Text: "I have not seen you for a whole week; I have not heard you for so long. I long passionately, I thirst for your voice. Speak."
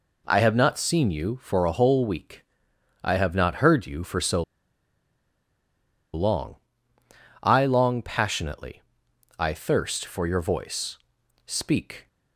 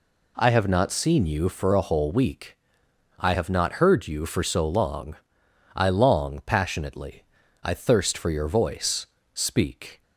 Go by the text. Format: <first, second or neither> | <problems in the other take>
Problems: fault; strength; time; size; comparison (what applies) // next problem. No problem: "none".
second | pauses between "so" and "long"; strong; at 4.4 s; 1.7 s long